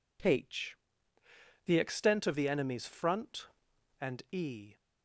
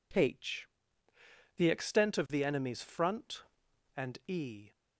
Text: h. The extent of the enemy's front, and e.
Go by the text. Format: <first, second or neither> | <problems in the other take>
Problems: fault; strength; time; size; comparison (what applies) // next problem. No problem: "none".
neither | none